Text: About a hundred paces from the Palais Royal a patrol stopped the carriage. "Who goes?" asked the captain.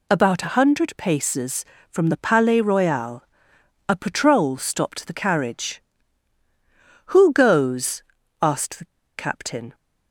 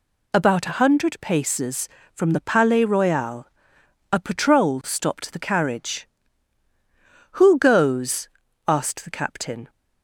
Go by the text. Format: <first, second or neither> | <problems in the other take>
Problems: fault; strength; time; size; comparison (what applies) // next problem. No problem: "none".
second | pauses between "Royal" and "a"; noticeable; at 3.2 s; 0.64 s long; noticeable in the second // pauses between "the" and "captain"; slight; at 8.8 s; 0.33 s long